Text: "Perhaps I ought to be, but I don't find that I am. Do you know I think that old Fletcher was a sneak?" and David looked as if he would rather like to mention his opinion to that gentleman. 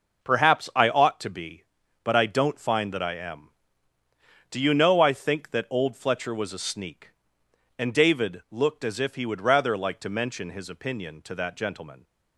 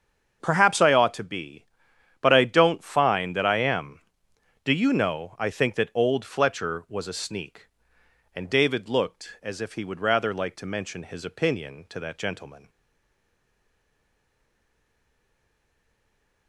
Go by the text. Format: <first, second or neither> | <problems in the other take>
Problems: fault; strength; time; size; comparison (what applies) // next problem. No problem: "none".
first | starts louder than the rest; until 1.4 s; 7 dB // stays silent after the last word; strong; from 12.6 s on; 3.8 s long